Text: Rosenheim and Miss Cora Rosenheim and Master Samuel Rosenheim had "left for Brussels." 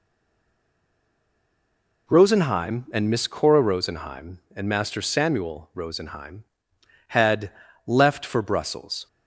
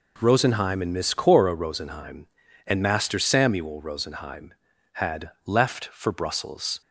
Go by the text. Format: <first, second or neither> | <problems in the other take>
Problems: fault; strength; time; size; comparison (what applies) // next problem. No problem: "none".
second | stays silent before the first word; noticeable; until 2.0 s; 2.0 s long // pauses between "had" and "left"; slight; at 7.5 s; 0.34 s long; slight in the second